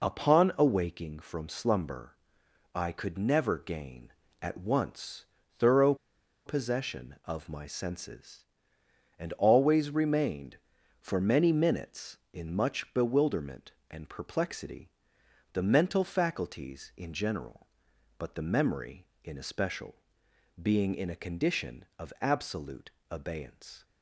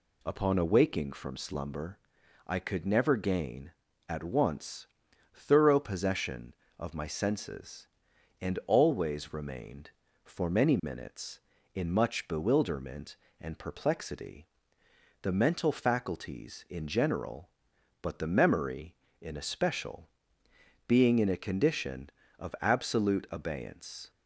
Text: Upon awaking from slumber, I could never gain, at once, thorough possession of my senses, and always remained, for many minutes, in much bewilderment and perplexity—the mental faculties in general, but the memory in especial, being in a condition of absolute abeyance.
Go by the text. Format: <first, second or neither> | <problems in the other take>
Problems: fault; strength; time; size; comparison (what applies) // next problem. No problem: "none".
second | pauses between "thorough" and "possession"; noticeable; at 5.9 s; 0.51 s long // pauses between "absolute" and "abeyance"; slight; at 22.9 s; 0.18 s long